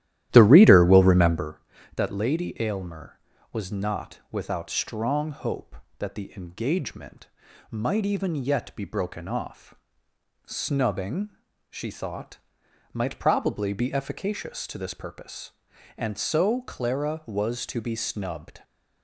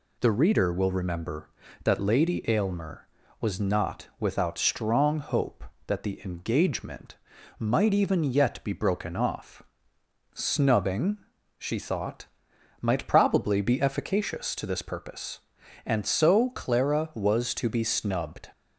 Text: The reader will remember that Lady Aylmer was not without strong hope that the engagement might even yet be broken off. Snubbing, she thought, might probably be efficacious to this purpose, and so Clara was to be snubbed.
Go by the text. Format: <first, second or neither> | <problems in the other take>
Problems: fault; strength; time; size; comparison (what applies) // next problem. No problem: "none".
second | starts louder than the rest; strong; until 1.5 s; 13 dB // pauses between "engagement" and "might"; at 7.2 s; 0.44 s long; also in the second